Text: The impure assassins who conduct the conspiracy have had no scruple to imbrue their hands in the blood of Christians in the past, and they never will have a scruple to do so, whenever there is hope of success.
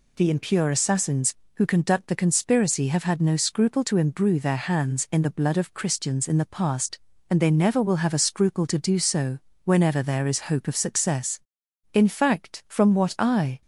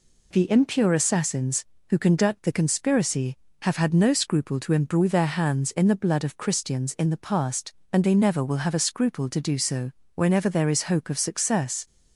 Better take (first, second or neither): second